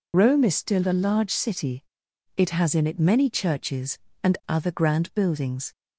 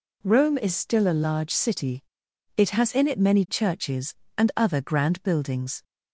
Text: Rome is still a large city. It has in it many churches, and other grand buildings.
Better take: second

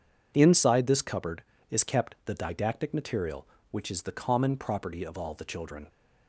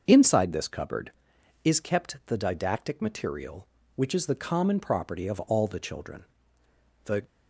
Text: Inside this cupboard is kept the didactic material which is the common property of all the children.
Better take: first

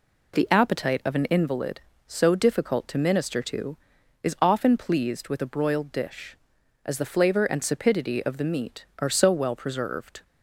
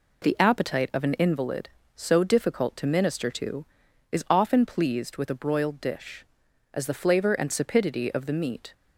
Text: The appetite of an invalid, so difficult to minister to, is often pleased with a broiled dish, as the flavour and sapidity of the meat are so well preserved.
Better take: first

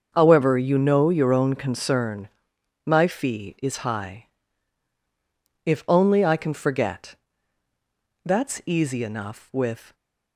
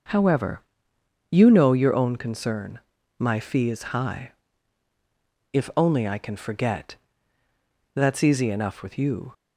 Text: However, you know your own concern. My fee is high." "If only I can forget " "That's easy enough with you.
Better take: second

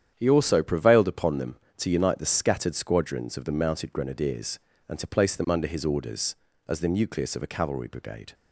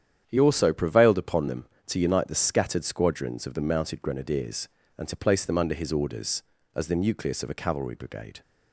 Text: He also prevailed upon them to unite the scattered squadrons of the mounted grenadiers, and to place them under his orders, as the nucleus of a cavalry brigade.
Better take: neither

